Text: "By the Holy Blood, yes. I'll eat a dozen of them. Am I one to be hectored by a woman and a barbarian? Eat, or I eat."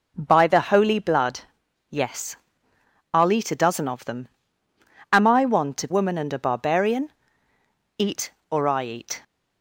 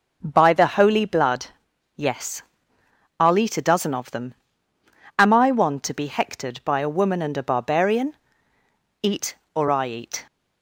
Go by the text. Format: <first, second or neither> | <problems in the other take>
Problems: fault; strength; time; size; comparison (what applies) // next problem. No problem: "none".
second | skips "be hectored by a"; at 5.8 s